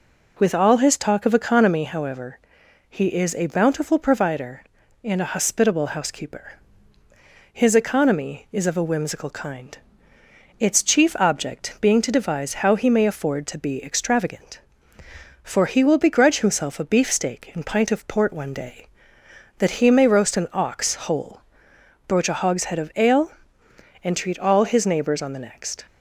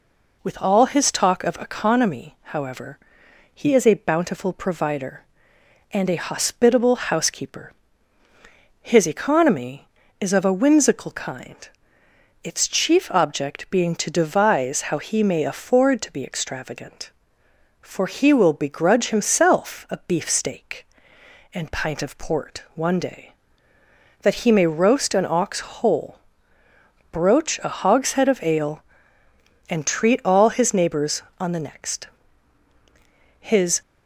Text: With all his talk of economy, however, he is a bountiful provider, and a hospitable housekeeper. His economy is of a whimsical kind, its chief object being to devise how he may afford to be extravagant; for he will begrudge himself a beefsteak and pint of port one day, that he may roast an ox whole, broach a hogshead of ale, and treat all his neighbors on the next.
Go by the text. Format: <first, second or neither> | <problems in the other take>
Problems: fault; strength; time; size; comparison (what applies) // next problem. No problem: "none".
first | goes on to say "His"; slight; from 33.4 s on; 0.40 s long